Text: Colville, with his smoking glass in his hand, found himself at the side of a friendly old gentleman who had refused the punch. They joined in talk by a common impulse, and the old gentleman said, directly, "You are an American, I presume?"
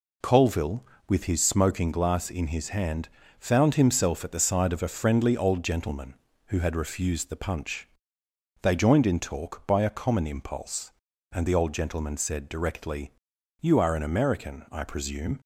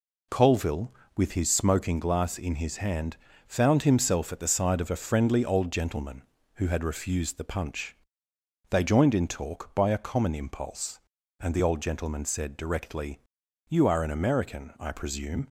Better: neither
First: none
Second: none

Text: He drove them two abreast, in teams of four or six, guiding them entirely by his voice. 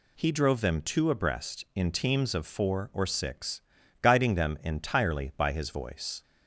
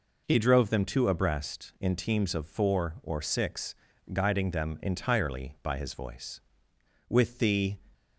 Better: first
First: none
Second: goes on to say "With the"; noticeable; from 7.0 s on; 0.68 s long

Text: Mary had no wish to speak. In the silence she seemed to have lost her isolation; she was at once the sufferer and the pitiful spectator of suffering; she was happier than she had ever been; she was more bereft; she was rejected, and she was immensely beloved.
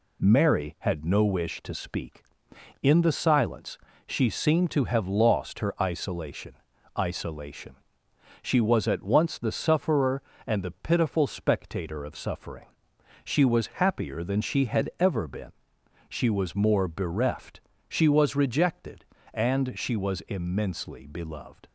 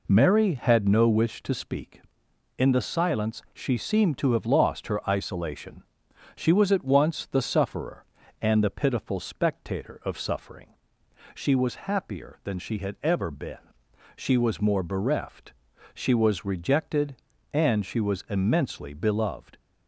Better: second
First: pauses between "silence" and "she"; slight; at 3.7 s; 0.26 s long // says "isolation" twice; at 6.9 s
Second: none

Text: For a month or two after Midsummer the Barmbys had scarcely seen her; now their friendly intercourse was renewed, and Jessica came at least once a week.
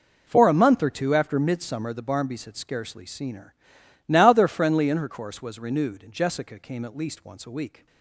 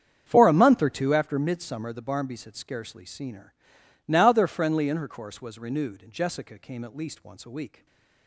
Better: first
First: none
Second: starts louder than the rest; strong; until 1.2 s; 8 dB // stays silent after the last word; slight; from 7.7 s on; 0.5 s long

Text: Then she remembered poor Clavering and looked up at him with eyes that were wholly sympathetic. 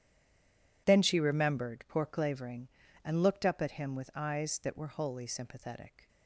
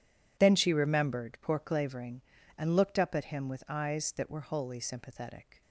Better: second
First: stays silent before the first word; slight; until 0.8 s; 0.8 s long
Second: none

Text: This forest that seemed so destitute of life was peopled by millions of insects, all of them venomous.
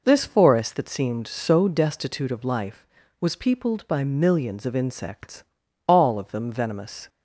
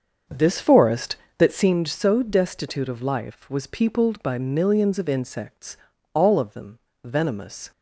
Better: first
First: none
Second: starts louder than the rest; until 1.7 s; 6.5 dB // pauses between "them" and "venomous"; slight; at 6.7 s; 0.26 s long

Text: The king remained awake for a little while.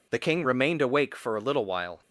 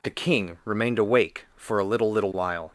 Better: first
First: none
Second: says "little" twice; at 2.0 s

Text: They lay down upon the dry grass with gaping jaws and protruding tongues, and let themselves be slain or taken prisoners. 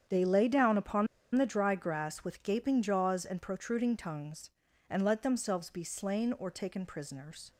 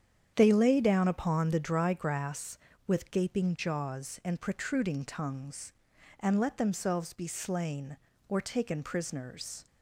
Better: second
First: starts louder than the rest; strong; until 1.3 s; 8.5 dB // pauses between "upon" and "the"; slight; at 1.0 s; 0.28 s long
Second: starts louder than the rest; strong; until 1.3 s; 8.5 dB

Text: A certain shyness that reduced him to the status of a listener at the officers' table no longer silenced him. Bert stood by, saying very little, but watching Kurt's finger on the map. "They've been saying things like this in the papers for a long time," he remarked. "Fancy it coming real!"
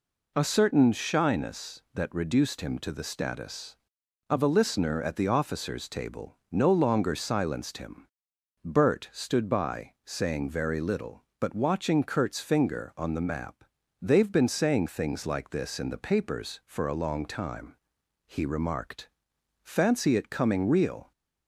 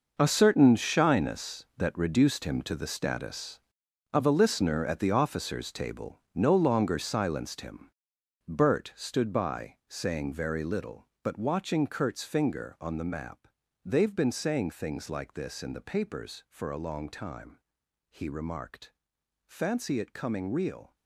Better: first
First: none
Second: gets quieter; strong; throughout; 13 dB

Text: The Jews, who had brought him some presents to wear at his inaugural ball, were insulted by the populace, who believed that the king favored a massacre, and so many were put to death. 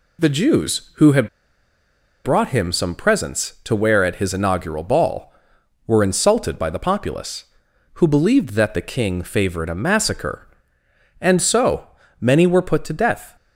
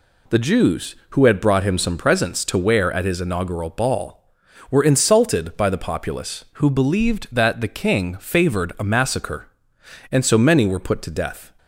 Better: second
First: pauses between "had" and "brought"; noticeable; at 1.2 s; 0.96 s long // pauses between "so" and "many"; slight; at 11.8 s; 0.34 s long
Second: none

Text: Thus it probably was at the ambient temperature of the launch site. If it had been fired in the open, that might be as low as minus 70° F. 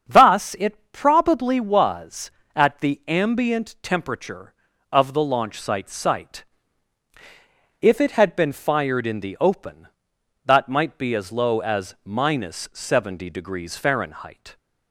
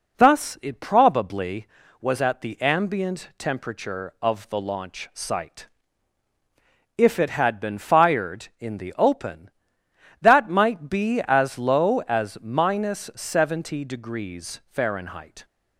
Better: second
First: starts louder than the rest; until 1.1 s; 7 dB // says "site" twice; at 5.8 s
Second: none

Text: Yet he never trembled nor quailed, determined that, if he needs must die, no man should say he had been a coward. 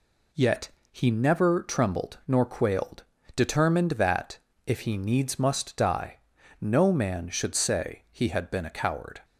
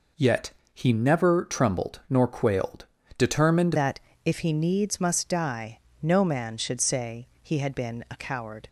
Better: first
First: pauses between "Yet" and "he"; slight; at 0.7 s; 0.20 s long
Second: pauses between "Yet" and "he"; slight; at 0.5 s; 0.20 s long // changes voice at "that"; from 3.7 s on; 4.9 s long

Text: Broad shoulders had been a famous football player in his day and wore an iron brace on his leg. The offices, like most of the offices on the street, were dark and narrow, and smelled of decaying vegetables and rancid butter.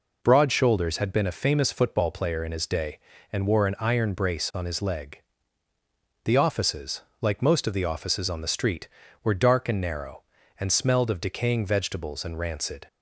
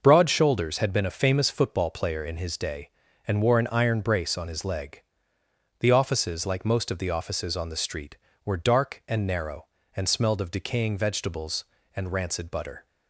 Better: second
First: stops before "butter"; at 12.8 s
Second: none

